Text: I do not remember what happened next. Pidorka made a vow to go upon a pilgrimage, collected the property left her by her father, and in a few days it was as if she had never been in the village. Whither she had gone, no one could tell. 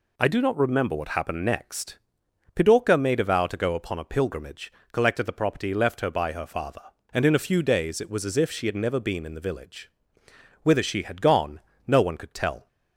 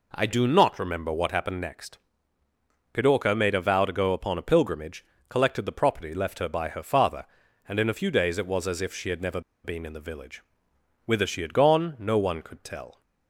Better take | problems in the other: first | pauses between "never" and "been"; slight; at 9.3 s; 0.24 s long

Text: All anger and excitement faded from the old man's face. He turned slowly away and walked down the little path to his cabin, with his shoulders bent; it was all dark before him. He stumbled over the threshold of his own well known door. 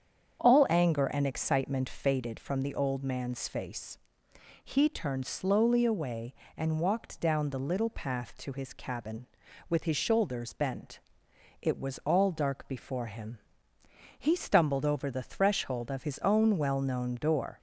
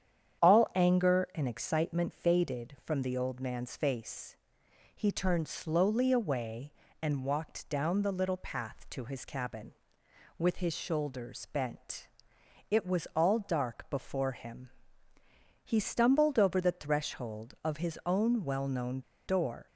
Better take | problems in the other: first | starts louder than the rest; strong; until 1.5 s; 9 dB; strong in the first // pauses between "known" and "door"; slight; at 19.0 s; 0.25 s long

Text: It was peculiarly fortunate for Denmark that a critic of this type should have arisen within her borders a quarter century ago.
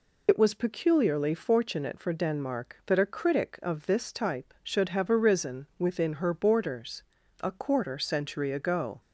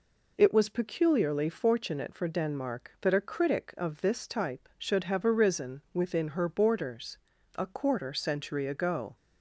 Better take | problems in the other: second | loses the start of "It"; at 0.2 s; 65 ms // pauses between "borders" and "a"; at 7.0 s; 0.40 s long; also in the second

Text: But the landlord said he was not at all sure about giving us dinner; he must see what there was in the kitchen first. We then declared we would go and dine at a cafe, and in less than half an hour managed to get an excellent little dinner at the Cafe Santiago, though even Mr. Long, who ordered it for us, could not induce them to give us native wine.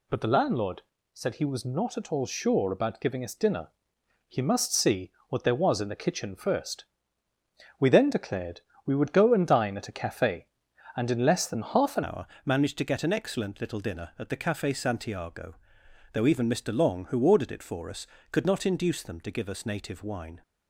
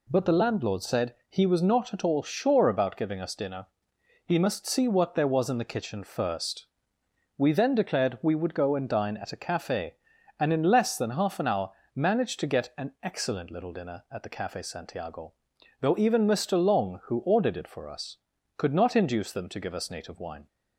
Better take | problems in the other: second | pauses between "landlord" and "said"; slight; at 0.8 s; 0.30 s long // pauses between "see" and "what"; slight; at 5.1 s; 0.18 s long // pauses between "declared" and "we"; slight; at 8.6 s; 0.24 s long // changes voice at "hour"; from 12.0 s on; 8.4 s long // pauses between "hour" and "managed"; slight; at 12.2 s; 0.18 s long; slight in the second

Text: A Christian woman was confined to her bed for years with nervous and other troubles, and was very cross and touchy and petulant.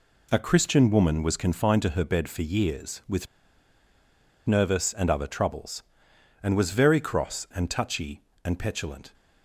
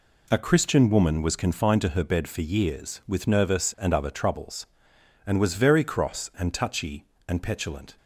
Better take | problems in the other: second | pauses between "with" and "nervous"; at 3.2 s; 1.2 s long

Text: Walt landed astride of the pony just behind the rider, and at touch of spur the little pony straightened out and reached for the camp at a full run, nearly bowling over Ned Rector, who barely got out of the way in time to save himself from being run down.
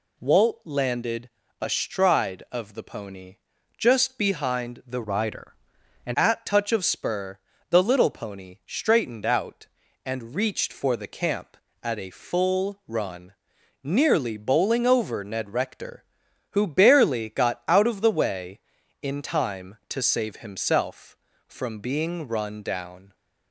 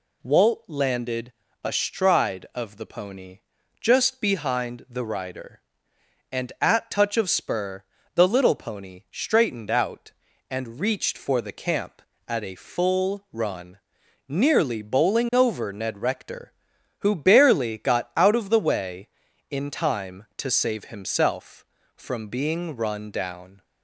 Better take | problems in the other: second | pauses between "landed" and "astride"; slight; at 1.2 s; 0.32 s long; slight in the second // pauses between "pony" and "just"; at 3.3 s; 0.40 s long; also in the second // changes voice from "rider" to "and"; from 5.0 to 6.1 s; 1.1 s long // pauses between "spur" and "the"; slight; at 7.3 s; 0.32 s long; slight in the second

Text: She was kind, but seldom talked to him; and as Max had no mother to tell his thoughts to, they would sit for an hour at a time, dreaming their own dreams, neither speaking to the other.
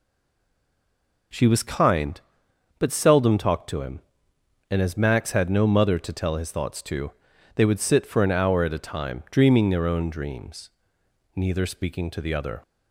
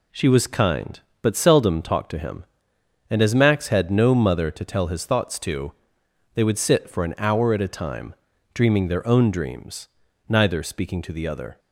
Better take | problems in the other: second | stays silent before the first word; noticeable; until 1.3 s; 1.3 s long

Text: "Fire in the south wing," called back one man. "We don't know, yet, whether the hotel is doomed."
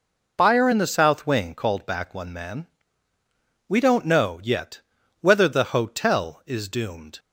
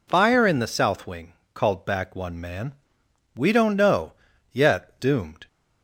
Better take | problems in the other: first | skips "whether the hotel is"; at 4.9 s

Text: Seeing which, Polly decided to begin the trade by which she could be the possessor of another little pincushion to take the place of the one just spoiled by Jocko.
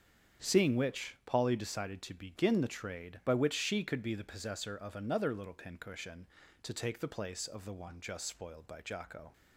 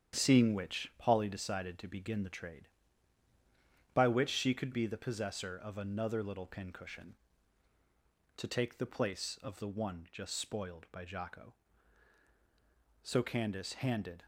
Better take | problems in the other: first | starts louder than the rest; strong; until 1.1 s; 9 dB; strong in the first // goes on to say "So Candace handed"; noticeable; from 13.0 s on; 1.2 s long

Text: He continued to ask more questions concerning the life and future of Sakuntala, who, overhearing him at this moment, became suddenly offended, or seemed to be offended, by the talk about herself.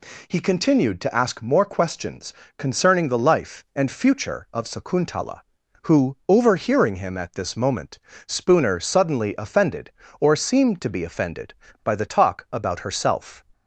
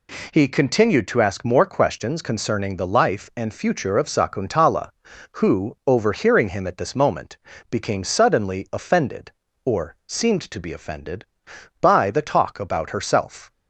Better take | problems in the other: second | pauses between "questions" and "concerning"; slight; at 2.3 s; 0.26 s long // says "spooner" for "became"; at 8.2 s

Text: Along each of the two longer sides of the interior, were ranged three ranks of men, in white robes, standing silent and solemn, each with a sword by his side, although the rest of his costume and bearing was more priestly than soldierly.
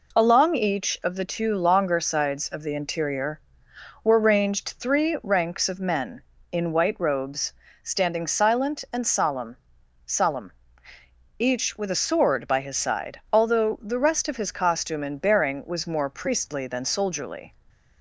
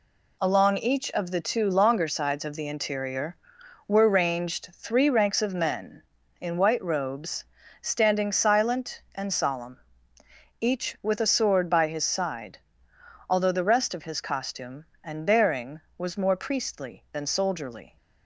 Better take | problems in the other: second | says "solemn" twice; at 10.0 s

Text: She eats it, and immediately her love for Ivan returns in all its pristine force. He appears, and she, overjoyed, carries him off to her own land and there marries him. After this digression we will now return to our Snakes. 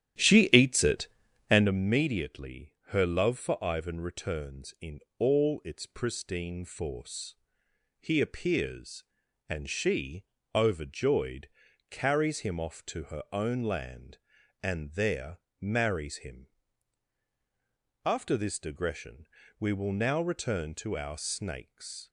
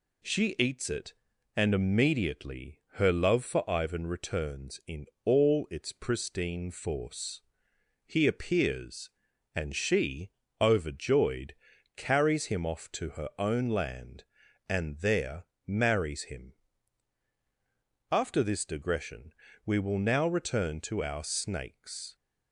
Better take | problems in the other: second | starts louder than the rest; strong; until 1.7 s; 11.5 dB // pauses between "in" and "all"; slight; at 4.9 s; 0.20 s long; slight in the second // pauses between "there" and "marries"; slight; at 15.3 s; 0.24 s long; slight in the second // pauses between "digression" and "we"; slight; at 19.2 s; 0.32 s long; slight in the second

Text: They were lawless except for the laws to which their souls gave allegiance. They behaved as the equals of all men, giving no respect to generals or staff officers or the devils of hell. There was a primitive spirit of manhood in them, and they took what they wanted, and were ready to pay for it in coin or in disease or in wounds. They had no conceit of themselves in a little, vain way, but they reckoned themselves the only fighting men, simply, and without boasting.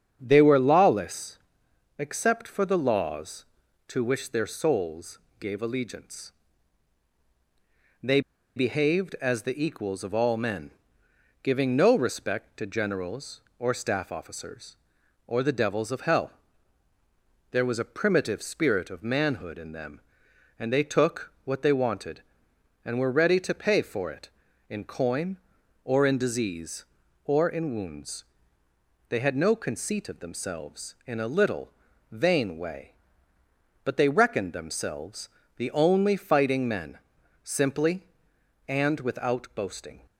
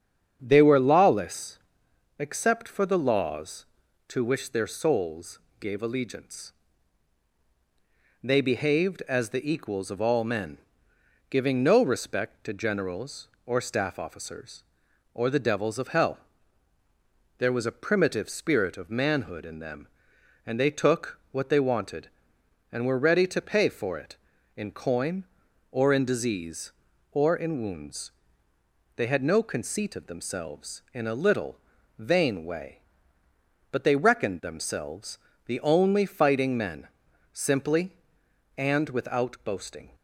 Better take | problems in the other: second | starts louder than the rest; strong; until 1.2 s; 8 dB; strong in the second // pauses between "lawless" and "except"; noticeable; at 1.3 s; 0.60 s long; noticeable in the second // pauses between "souls" and "gave"; slight; at 5.1 s; 0.20 s long; slight in the second // pauses between "They" and "behaved"; slight; at 8.2 s; 0.36 s long // pauses between "themselves" and "the"; slight; at 35.2 s; 0.28 s long; slight in the second

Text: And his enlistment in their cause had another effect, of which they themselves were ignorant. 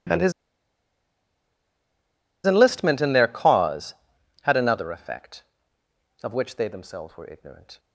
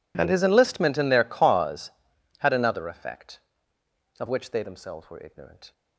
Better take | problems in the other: second | pauses between "his" and "enlistment"; strong; at 0.3 s; 2.1 s long

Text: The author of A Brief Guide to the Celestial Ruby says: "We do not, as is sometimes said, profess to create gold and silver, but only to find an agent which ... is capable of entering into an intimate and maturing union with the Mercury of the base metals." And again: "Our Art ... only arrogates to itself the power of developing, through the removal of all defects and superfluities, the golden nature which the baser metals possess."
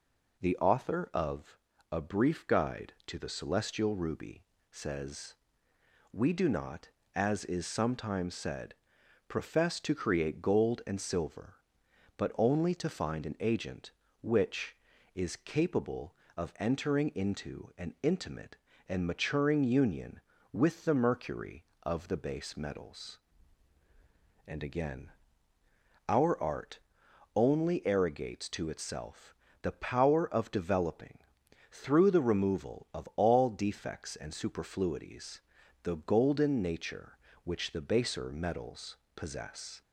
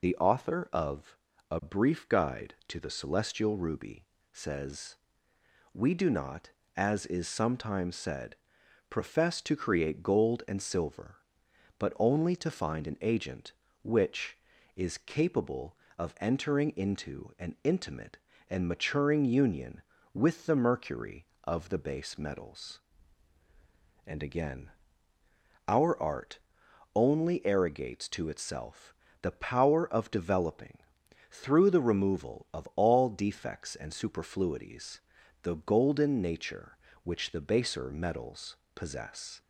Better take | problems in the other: first | loses the start of "The"; at 0.0 s; 45 ms // pauses between "of" and "A"; slight; at 1.1 s; 0.32 s long; slight in the first // pauses between "Ruby" and "says"; slight; at 4.0 s; 0.26 s long; slight in the first // pauses between "itself" and "the"; slight; at 28.9 s; 0.28 s long; slight in the first // pauses between "metals" and "possess"; slight; at 38.5 s; 0.20 s long; slight in the first

